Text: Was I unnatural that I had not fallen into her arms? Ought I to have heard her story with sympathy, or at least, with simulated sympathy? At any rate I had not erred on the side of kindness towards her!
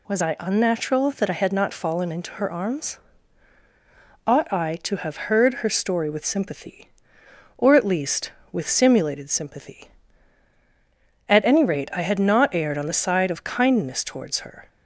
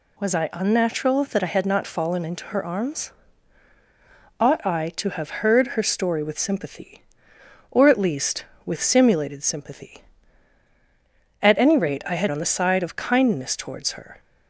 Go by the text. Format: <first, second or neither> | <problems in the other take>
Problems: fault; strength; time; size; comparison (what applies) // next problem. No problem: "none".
first | skips "not erred"; at 12.2 s